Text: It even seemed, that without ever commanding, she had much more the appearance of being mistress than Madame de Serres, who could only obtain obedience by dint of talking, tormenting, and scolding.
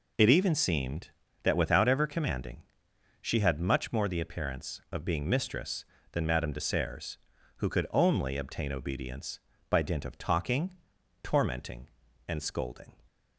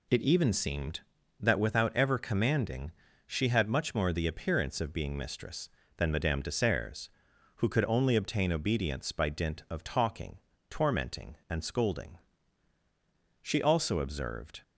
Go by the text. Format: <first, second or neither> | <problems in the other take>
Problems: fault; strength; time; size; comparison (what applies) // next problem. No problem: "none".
first | goes on to say "She also observed"; noticeable; from 13.4 s on; 1.2 s long